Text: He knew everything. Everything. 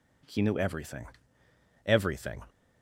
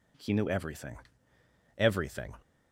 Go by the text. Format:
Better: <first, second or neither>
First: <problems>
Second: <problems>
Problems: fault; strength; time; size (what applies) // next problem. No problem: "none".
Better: neither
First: none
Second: none